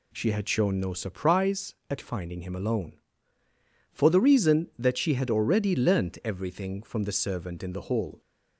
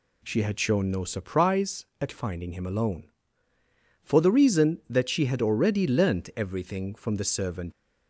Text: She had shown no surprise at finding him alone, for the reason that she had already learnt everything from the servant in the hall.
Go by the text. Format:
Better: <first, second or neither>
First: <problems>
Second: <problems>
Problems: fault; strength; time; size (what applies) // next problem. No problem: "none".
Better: first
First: none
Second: stops before "in the hall"; at 7.7 s